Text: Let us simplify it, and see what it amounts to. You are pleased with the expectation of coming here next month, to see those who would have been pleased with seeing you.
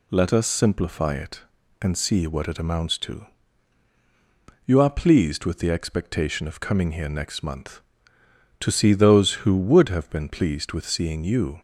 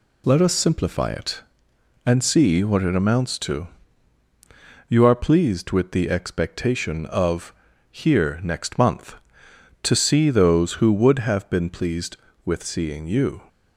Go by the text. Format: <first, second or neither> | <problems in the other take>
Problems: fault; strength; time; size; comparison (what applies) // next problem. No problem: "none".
first | skips "coming"; at 7.7 s